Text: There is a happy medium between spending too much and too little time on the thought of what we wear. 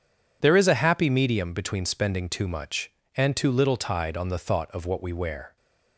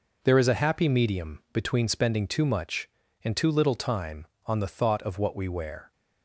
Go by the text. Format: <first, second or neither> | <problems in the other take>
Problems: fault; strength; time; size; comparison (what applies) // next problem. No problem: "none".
second | says "tide" for "time"; at 3.7 s